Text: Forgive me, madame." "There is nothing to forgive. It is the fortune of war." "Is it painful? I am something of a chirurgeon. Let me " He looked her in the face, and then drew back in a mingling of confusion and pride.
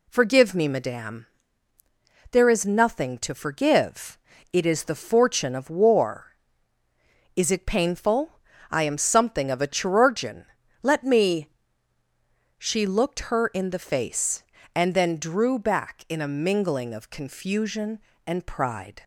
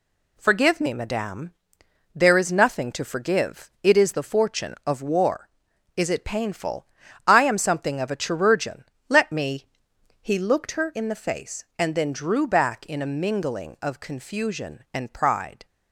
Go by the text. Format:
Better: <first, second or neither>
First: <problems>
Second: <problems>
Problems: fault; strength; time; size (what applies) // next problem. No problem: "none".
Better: second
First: says "She" for "He"; at 12.5 s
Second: none